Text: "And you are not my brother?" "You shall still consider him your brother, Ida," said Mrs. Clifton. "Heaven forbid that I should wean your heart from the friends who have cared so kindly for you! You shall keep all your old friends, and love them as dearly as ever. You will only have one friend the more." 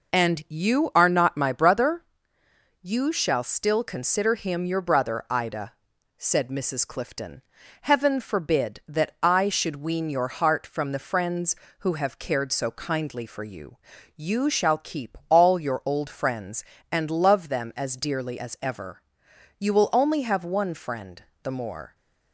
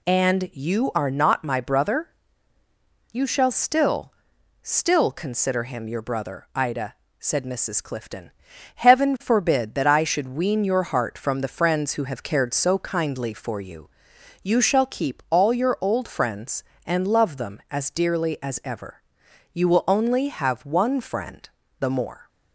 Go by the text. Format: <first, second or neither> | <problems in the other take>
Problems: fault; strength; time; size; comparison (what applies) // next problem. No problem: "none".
first | says "still" twice; at 4.6 s // pauses between "friend" and "the"; slight; at 21.4 s; 0.32 s long; slight in the first